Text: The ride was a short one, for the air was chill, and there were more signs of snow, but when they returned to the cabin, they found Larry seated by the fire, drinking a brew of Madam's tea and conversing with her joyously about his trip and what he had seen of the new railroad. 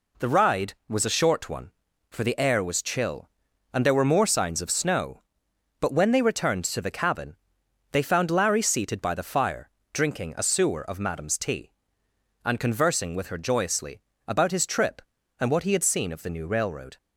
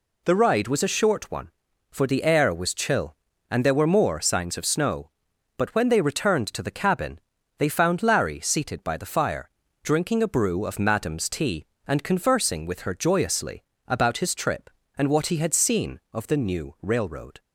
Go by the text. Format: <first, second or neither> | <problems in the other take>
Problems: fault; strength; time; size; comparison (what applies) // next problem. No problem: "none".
second | says "sewer" for "brew"; at 10.4 s // pauses between "joyously" and "about"; slight; at 13.9 s; 0.28 s long; slight in the second